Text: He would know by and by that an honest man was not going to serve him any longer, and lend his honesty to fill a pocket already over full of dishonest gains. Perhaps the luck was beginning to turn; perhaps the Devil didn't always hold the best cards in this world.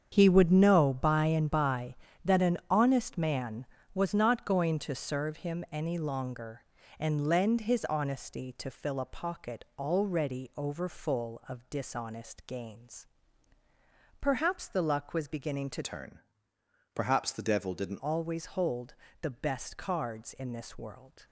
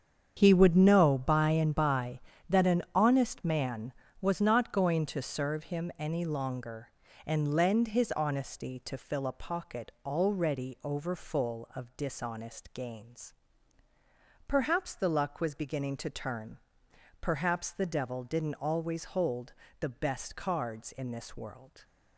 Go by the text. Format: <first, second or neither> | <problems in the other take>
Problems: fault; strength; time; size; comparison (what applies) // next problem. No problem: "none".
second | starts louder than the rest; strong; until 1.1 s; 7.5 dB; strong in the second // changes voice from "turn" to "didn't"; from 15.8 to 17.9 s; 2.1 s long // pauses between "hold" and "the"; slight; at 18.9 s; 0.28 s long; slight in the second